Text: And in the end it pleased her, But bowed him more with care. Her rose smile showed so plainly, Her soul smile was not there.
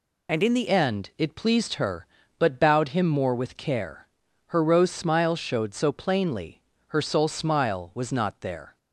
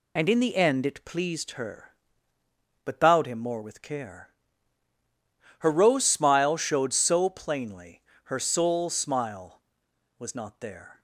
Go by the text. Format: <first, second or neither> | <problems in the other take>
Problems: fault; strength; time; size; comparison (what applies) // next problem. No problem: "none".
second | changes voice at "end"; from 0.6 s on; 8.1 s long